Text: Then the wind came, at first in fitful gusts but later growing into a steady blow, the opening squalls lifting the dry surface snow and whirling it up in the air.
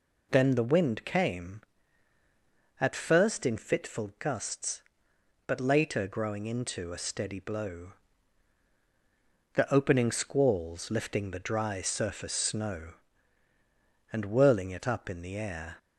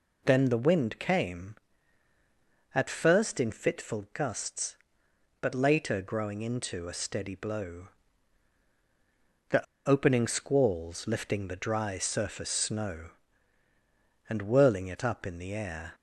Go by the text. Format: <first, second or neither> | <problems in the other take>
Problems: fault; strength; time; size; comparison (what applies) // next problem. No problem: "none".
first | pauses between "the" and "opening"; slight; at 9.6 s; 0.23 s long